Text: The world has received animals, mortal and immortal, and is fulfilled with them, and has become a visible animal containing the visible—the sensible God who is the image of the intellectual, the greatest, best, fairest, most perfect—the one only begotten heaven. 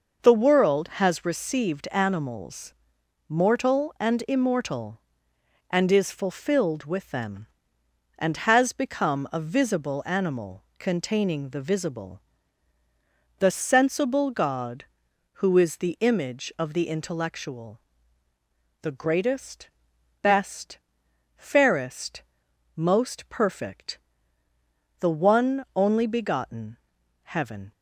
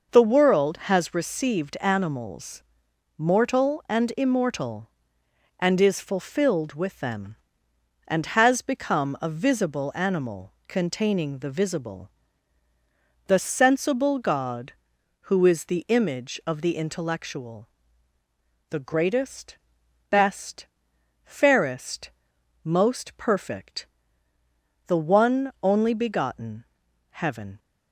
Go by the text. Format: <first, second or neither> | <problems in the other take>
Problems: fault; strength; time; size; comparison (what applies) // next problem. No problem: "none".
neither | pauses between "animal" and "containing"; slight; the same in both // pauses between "begotten" and "heaven"; noticeable; the same in both